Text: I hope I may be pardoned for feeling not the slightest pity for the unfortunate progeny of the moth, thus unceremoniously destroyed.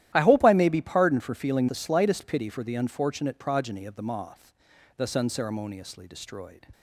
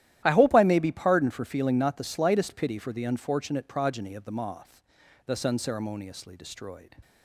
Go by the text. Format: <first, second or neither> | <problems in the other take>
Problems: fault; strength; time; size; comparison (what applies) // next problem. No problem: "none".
second | starts louder than the rest; strong; until 1.1 s; 13 dB; strong in the second // skips "not"; at 1.6 s